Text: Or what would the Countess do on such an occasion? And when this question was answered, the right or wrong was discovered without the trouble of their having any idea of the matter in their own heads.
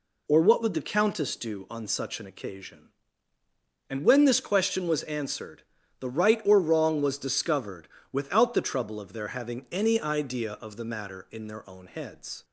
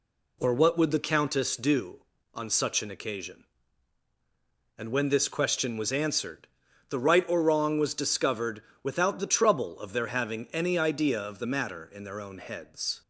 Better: neither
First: pauses between "discovered" and "without"; slight; at 7.8 s; 0.22 s long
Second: pauses between "discovered" and "without"; slight; at 8.6 s; 0.20 s long

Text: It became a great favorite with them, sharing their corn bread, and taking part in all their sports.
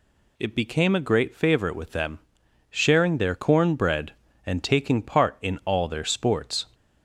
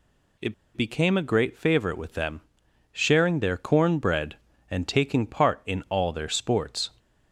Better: first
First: none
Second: pauses between "It" and "became"; slight; at 0.5 s; 0.21 s long

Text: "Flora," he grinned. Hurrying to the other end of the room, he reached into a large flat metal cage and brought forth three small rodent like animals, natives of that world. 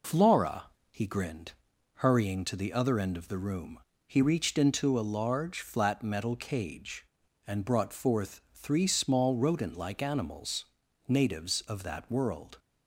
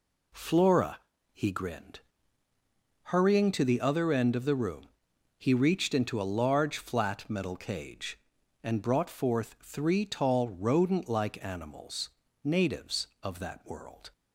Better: first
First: none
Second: says "tall" for "small"; at 10.0 s

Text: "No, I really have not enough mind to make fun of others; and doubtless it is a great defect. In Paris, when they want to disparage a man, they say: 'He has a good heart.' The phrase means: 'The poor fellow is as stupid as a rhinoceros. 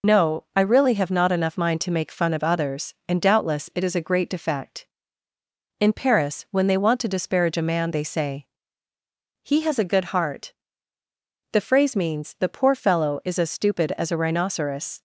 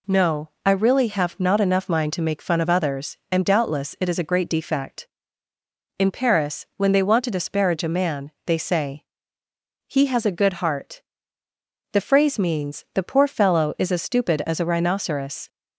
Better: second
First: loses the start of "No"; at 0.0 s; 50 ms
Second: none

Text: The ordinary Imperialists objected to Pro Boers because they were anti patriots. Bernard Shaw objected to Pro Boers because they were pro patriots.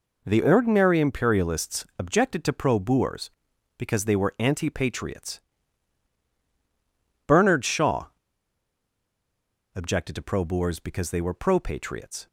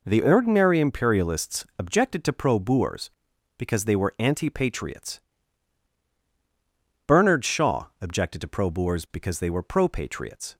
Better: second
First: pauses between "Shaw" and "objected"; strong; at 8.0 s; 1.6 s long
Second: none

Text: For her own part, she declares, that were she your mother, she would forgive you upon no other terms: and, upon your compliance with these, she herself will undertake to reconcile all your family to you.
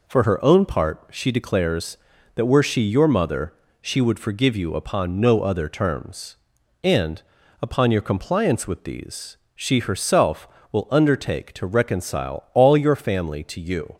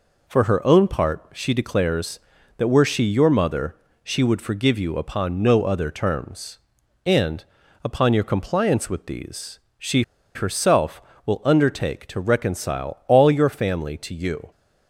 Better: first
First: none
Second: pauses between "she" and "herself"; slight; at 10.0 s; 0.33 s long

